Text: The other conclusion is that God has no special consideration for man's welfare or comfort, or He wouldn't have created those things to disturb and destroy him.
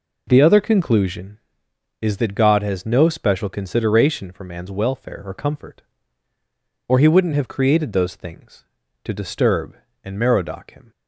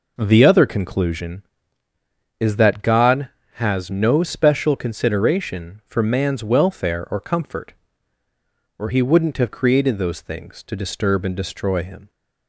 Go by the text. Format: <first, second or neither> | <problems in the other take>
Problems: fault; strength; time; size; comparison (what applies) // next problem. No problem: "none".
second | says "merodach" for "destroy"; at 10.1 s